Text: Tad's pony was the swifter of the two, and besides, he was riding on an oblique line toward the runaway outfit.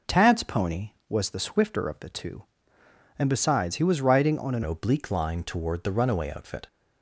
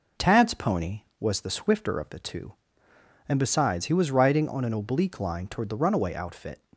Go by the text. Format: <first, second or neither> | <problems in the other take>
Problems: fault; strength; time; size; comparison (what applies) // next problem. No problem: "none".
second | changes voice at "oblique"; from 4.6 s on; 2.0 s long